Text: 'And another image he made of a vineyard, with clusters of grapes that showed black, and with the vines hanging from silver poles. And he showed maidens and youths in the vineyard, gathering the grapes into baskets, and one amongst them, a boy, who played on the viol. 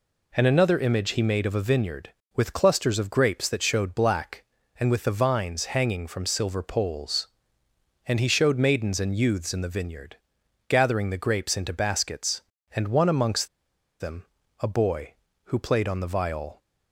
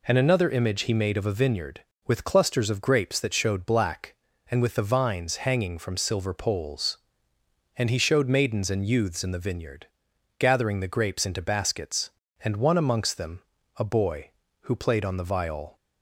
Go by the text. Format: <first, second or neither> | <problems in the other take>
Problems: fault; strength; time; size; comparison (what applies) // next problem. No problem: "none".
second | pauses between "amongst" and "them"; noticeable; at 13.4 s; 0.52 s long